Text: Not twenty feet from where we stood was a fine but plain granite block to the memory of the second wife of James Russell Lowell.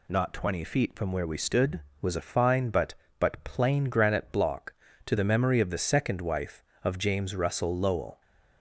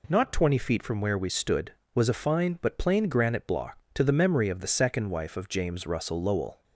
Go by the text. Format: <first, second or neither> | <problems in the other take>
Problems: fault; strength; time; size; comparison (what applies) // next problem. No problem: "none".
second | says "but" twice; at 3.1 s